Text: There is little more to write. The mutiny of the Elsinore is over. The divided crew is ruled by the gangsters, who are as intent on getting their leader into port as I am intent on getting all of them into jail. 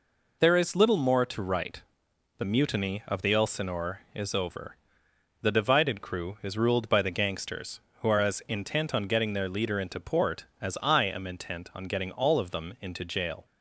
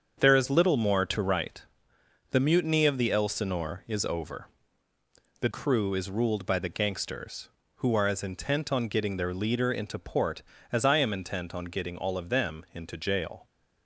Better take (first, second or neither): first